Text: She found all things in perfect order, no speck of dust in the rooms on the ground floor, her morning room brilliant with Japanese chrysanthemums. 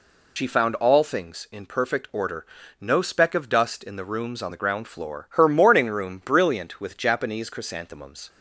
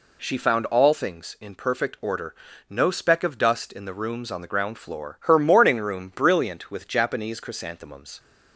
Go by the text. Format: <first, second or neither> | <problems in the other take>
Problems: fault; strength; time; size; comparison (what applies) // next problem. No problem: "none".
second | loses the start of "She"; at 0.3 s; 70 ms